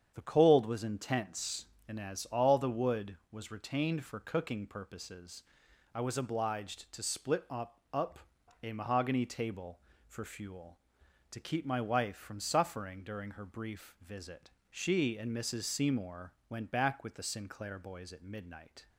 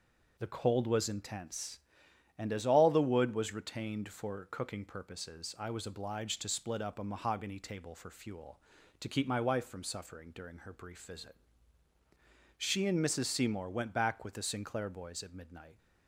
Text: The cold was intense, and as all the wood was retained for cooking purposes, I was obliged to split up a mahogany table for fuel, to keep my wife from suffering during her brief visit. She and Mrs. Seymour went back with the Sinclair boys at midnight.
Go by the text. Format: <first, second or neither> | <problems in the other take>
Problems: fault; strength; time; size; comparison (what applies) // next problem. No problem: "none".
second | starts louder than the rest; strong; until 1.1 s; 8 dB // says "up" twice; at 7.9 s // pauses between "Seymour" and "went"; slight; at 16.3 s; 0.16 s long